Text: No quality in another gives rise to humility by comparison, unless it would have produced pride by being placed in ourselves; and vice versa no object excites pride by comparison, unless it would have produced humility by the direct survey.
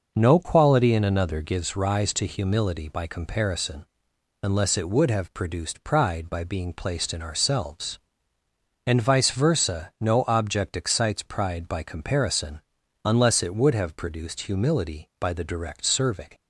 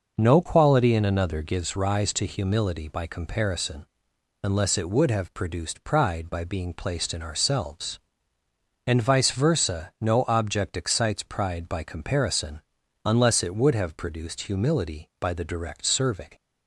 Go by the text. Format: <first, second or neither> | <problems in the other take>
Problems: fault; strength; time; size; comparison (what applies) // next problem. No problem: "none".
neither | none